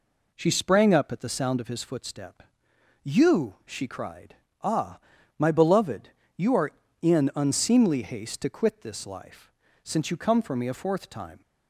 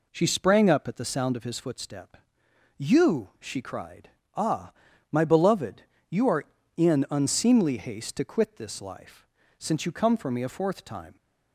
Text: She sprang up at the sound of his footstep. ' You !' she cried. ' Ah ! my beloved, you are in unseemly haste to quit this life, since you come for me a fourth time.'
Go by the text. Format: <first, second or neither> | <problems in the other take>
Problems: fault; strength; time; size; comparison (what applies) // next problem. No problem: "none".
neither | none